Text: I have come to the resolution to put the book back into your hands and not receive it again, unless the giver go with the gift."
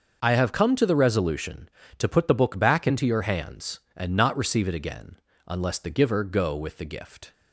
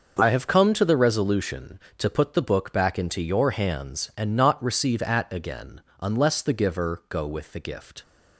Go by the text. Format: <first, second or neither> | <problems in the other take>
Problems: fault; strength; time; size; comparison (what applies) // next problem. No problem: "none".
first | starts louder than the rest; until 1.2 s; 6.5 dB; also in the first // says "at" for "it"; at 5.0 s